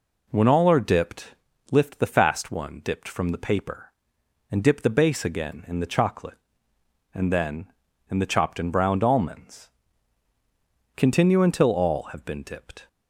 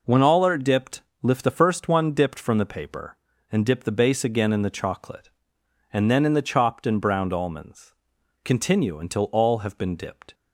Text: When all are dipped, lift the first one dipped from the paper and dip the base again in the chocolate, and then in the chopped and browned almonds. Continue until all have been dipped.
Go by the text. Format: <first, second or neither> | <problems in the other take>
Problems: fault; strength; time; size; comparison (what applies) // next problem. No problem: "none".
second | says "fast" for "first"; at 2.0 s